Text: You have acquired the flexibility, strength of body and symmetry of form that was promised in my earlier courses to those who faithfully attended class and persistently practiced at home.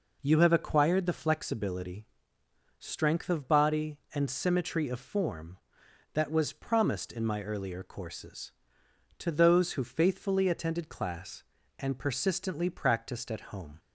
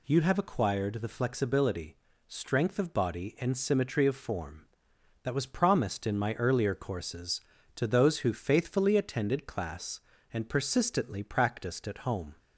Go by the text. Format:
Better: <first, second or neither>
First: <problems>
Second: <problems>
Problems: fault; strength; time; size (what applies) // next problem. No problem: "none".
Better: neither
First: none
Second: none